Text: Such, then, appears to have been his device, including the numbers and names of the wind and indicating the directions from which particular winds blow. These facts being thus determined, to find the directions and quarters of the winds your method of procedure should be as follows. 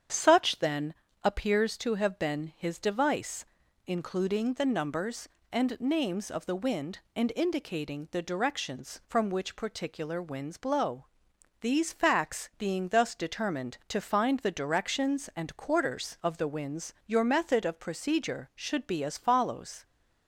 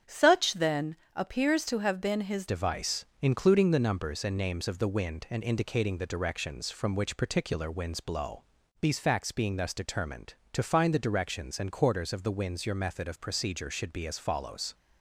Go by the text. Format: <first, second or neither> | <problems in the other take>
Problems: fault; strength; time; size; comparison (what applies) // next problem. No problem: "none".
first | starts louder than the rest; strong; until 1.2 s; 8 dB; strong in the first // changes voice at "device"; from 2.4 s on; 12.3 s long